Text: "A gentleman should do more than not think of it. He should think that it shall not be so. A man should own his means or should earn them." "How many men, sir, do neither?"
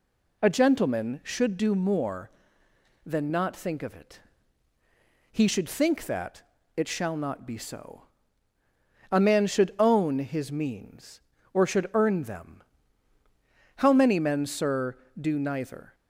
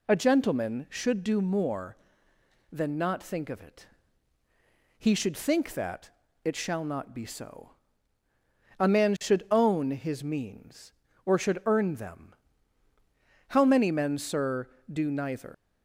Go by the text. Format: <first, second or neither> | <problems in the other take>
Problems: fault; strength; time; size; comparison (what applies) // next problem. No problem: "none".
first | pauses between "that" and "it"; slight; at 6.1 s; 0.34 s long; slight in the first // leaves "neither" unfinished; at 15.5 s; 115 ms